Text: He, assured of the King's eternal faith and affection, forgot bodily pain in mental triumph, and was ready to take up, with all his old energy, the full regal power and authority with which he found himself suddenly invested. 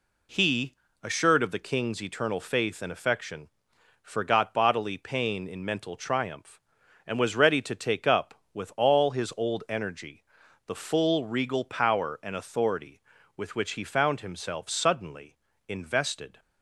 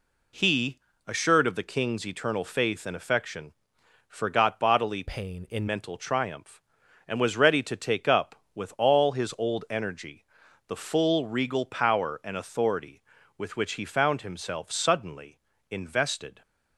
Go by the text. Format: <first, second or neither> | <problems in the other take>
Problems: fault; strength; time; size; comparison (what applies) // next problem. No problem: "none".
first | changes voice from "pain" to "in"; from 5.0 to 5.6 s; 0.6 s long // pauses between "suddenly" and "invested"; slight; at 15.3 s; 0.32 s long; slight in the first